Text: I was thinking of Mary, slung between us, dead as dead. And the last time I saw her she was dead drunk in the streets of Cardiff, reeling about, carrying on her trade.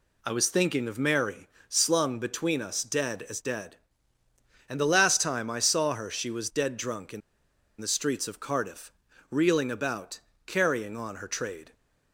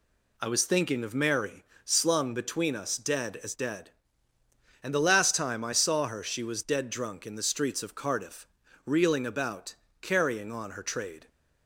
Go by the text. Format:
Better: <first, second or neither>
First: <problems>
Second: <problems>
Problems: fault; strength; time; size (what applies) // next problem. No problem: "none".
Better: second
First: pauses between "in" and "the"; noticeable; at 7.2 s; 0.60 s long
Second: none